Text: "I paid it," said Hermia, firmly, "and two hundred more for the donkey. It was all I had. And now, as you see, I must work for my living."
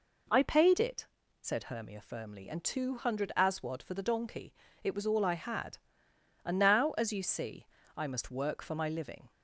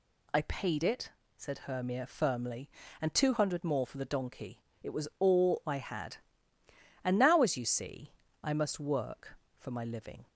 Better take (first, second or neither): second